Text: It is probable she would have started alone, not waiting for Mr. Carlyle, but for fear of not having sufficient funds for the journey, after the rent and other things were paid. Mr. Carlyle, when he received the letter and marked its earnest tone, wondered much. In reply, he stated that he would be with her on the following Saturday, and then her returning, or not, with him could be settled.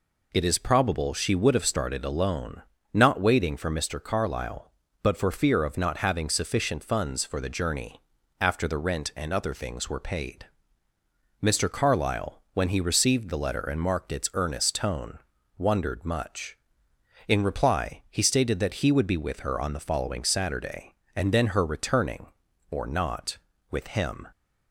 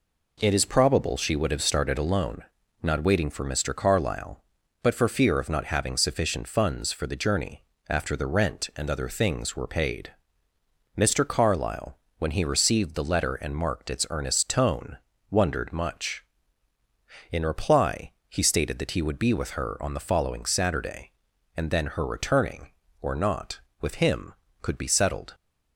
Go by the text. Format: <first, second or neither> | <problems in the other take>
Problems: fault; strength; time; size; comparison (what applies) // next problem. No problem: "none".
second | stops before "could be settled"; at 24.3 s